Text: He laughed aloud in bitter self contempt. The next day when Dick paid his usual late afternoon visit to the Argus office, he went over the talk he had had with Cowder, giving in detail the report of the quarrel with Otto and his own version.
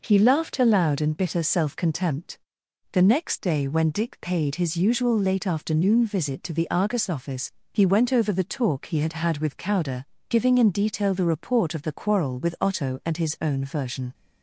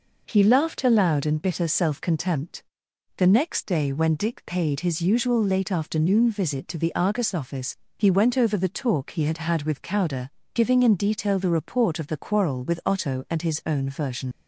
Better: first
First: none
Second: leaves "version" unfinished; at 14.3 s; 65 ms

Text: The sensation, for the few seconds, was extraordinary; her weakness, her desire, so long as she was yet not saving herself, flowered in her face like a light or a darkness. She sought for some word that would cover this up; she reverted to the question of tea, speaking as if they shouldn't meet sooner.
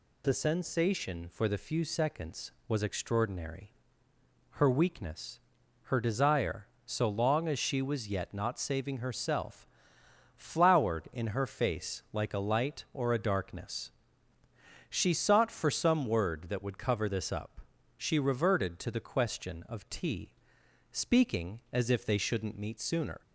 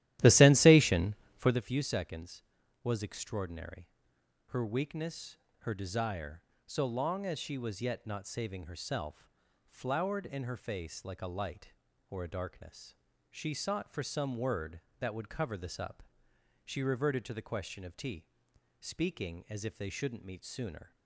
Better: first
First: none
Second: starts louder than the rest; strong; until 1.6 s; 13.5 dB

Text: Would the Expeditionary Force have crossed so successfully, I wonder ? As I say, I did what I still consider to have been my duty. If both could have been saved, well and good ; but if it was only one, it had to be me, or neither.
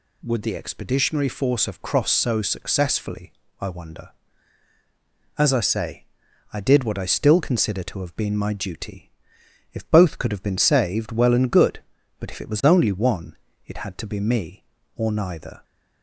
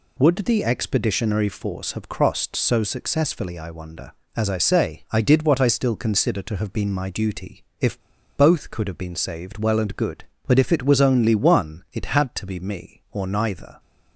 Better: first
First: none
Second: pauses between "If" and "both"; at 8.0 s; 0.36 s long

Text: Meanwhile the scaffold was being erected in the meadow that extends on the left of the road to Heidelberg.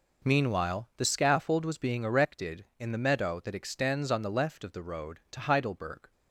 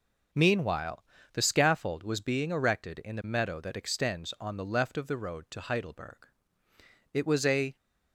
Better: first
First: none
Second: pauses between "Meanwhile" and "the"; slight; at 1.0 s; 0.30 s long // goes on to say "It was a"; noticeable; from 7.1 s on; 0.64 s long

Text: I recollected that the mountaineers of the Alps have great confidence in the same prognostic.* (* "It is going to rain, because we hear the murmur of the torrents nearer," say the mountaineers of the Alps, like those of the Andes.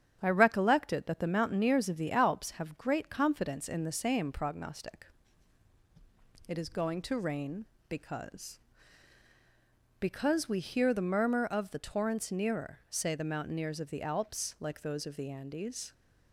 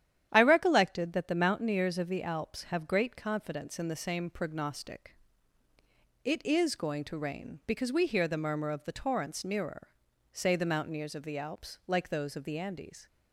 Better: second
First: starts louder than the rest; strong; until 1.2 s; 10 dB // says "because" twice; at 10.0 s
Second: starts louder than the rest; strong; until 1.3 s; 11 dB

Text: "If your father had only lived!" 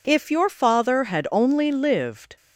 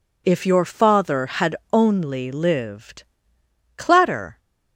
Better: first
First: none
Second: pauses between "had" and "only"; slight; at 1.5 s; 0.16 s long // goes on to say "Clatter"; noticeable; from 3.7 s on; 0.62 s long

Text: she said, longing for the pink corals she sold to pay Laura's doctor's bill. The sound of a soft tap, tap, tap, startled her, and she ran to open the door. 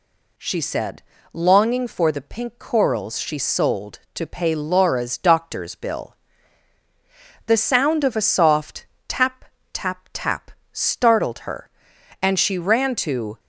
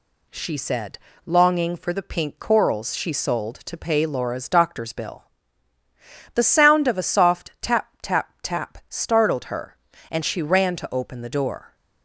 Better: second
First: pauses between "soft" and "tap"; slight; at 8.8 s; 0.22 s long // stops before "open the door"; at 13.3 s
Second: none

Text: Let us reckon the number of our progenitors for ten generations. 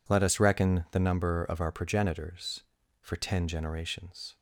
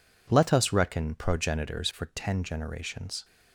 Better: first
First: none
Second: skips "the number of our"; at 1.1 s

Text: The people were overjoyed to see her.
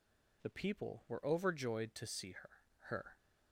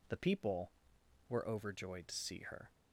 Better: second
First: says "her" twice; at 2.8 s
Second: none

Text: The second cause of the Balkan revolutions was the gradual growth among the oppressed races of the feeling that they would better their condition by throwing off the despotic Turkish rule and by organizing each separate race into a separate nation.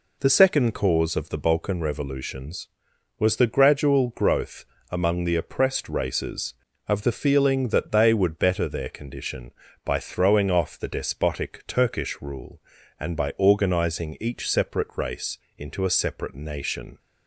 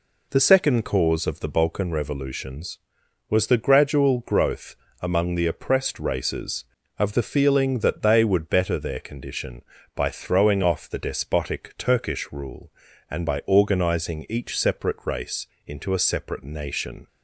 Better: neither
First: pauses between "growth" and "among"; slight; at 4.6 s; 0.26 s long // pauses between "race" and "into"; slight; at 15.3 s; 0.20 s long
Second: pauses between "growth" and "among"; slight; at 4.7 s; 0.26 s long // pauses between "race" and "into"; slight; at 15.4 s; 0.20 s long

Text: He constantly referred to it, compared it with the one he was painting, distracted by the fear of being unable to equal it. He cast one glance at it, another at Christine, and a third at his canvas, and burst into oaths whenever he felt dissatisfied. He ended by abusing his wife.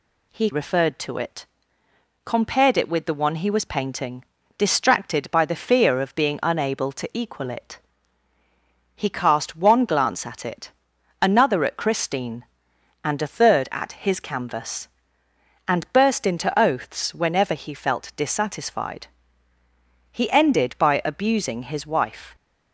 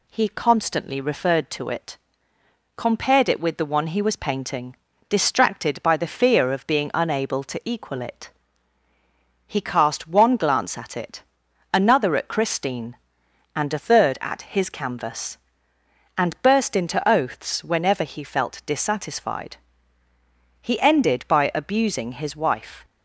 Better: second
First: skips "constantly"; at 0.5 s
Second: none

